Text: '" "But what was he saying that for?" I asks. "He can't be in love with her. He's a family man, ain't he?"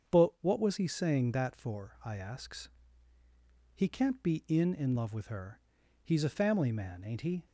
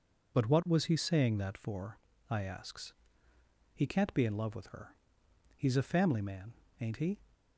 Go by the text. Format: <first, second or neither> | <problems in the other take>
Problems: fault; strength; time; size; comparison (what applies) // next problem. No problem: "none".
second | starts louder than the rest; strong; until 1.2 s; 7 dB // says "in" twice; at 4.7 s